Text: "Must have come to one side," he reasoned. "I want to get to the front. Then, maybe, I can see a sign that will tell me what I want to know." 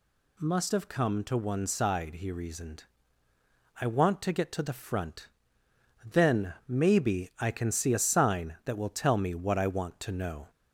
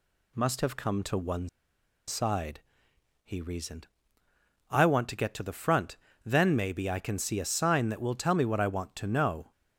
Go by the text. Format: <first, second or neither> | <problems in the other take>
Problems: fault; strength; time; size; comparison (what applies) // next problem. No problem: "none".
first | pauses between "one" and "side"; noticeable; at 1.4 s; 0.60 s long